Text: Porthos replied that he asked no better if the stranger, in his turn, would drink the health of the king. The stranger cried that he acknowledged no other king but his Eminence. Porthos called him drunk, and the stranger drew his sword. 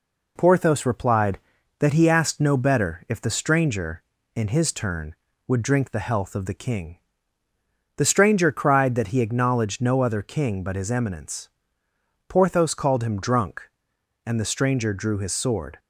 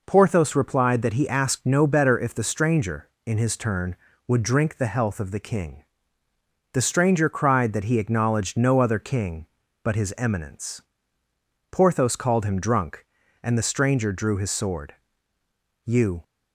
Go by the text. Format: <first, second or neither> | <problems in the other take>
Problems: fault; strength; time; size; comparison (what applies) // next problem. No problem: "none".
first | goes on to say "You"; slight; from 15.8 s on; 0.38 s long